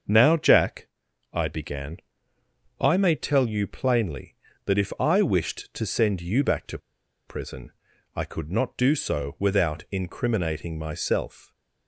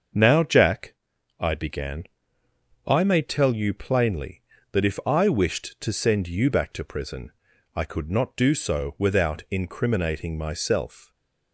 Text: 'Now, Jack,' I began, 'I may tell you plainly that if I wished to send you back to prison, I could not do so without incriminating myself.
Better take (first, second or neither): second